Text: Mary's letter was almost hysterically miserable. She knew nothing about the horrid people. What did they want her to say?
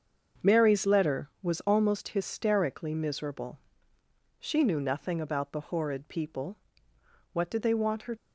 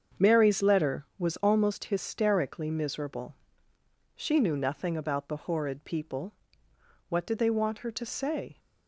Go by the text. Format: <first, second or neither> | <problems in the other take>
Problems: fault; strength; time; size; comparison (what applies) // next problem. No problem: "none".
second | starts louder than the rest; until 1.5 s; 6.5 dB; also in the second // stops before "to say"; at 8.1 s